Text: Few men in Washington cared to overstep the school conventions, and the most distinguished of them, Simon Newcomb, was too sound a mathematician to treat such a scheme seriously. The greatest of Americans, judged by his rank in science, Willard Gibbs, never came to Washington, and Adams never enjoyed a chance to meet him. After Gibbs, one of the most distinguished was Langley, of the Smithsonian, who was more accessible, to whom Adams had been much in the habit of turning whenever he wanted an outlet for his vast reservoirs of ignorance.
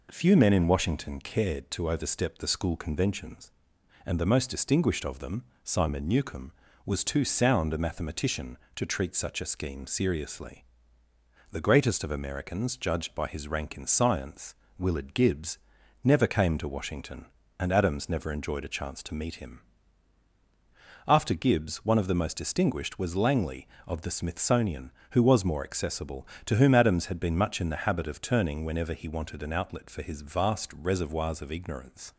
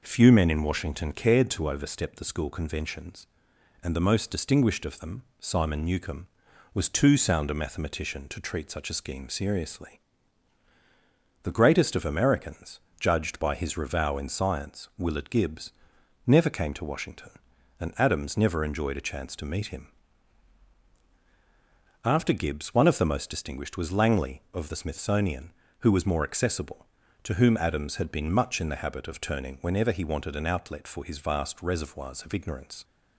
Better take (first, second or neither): first